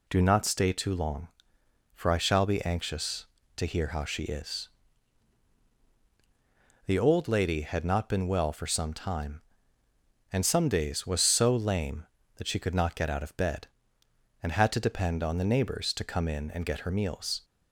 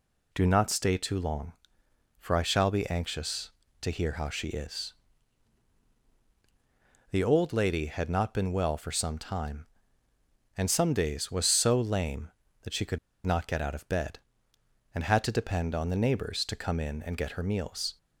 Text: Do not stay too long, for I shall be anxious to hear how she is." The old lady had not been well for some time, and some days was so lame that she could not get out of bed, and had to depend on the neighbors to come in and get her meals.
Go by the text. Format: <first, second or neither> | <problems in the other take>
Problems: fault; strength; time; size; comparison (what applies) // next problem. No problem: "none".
first | pauses between "could" and "not"; slight; at 12.9 s; 0.28 s long